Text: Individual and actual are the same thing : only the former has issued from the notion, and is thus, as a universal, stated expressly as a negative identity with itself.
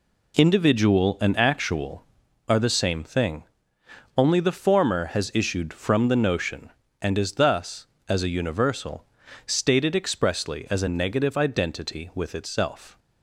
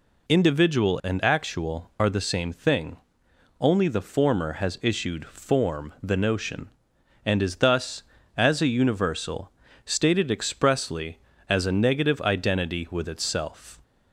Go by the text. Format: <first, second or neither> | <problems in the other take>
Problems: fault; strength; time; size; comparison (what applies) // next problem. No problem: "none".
first | says "form" for "from"; at 5.2 s